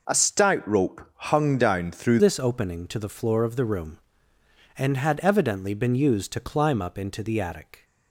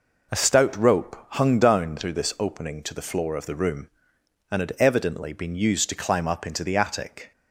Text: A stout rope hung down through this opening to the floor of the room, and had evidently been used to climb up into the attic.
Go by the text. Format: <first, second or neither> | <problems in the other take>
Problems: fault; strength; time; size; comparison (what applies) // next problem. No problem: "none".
second | changes voice at "this"; from 2.1 s on; 5.7 s long